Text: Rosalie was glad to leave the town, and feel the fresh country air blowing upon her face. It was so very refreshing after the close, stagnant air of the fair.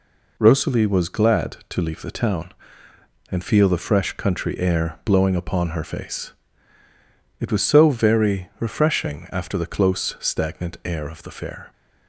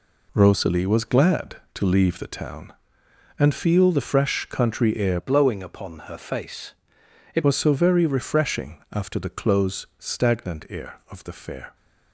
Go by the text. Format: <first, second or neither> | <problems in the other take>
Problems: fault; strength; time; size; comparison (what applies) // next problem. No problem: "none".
first | changes voice from "blowing" to "It"; from 5.1 to 7.4 s; 2.3 s long